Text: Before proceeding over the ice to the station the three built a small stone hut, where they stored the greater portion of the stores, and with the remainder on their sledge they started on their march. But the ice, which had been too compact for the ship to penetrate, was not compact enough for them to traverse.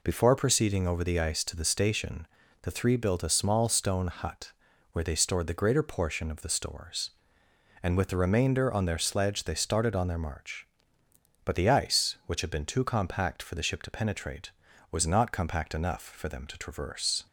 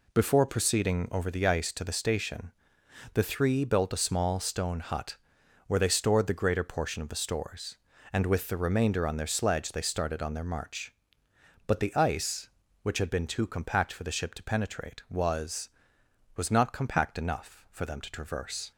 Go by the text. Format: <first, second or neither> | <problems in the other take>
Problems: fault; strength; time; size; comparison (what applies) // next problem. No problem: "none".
first | pauses between "station" and "the"; noticeable; at 2.5 s; 0.62 s long; slight in the first // says "was" twice; at 16.3 s